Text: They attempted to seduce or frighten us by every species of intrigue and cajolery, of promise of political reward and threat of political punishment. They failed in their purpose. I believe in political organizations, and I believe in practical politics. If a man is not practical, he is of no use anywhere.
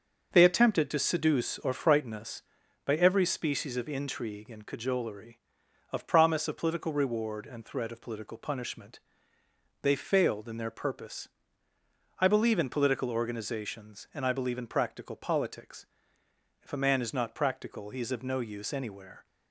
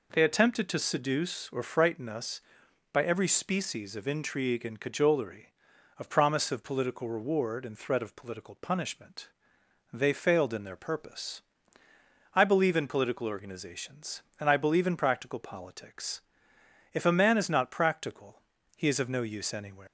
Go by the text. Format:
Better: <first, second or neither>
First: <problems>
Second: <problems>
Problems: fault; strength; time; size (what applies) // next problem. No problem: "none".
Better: first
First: none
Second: leaves "anywhere" unfinished; at 19.8 s; 155 ms